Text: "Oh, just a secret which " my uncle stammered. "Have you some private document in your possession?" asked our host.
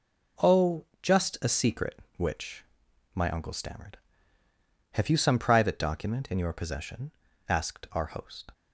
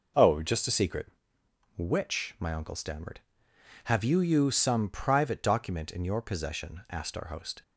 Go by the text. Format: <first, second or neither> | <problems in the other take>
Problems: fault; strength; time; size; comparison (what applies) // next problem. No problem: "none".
first | says "you" twice; at 4.1 s